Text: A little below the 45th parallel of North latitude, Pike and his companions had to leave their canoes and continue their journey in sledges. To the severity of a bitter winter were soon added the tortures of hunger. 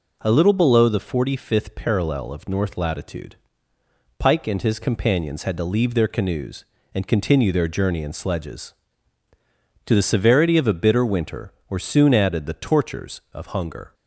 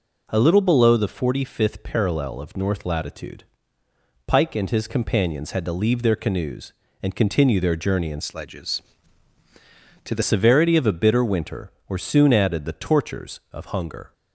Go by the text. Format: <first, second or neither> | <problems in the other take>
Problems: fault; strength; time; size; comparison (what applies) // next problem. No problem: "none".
first | changes voice from "sledges" to "the"; from 8.2 to 10.2 s; 2.0 s long